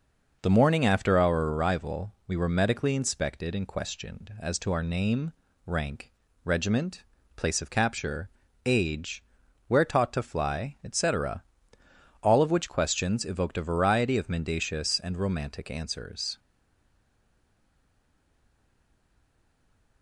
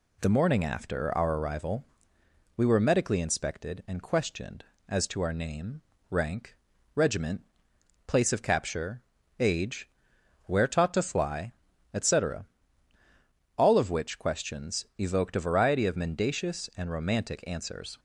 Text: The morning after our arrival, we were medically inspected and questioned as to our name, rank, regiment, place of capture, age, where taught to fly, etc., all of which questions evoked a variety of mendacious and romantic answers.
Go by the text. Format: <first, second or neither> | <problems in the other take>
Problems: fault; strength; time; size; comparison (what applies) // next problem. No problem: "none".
second | stays silent after the last word; strong; from 16.3 s on; 3.7 s long